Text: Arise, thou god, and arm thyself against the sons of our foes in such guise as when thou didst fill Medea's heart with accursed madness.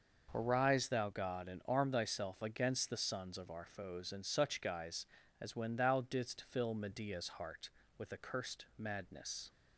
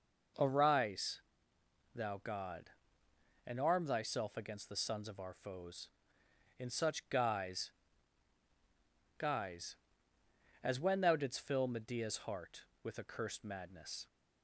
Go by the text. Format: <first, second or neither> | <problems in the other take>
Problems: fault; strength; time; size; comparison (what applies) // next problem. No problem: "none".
first | says "guise" twice; at 9.1 s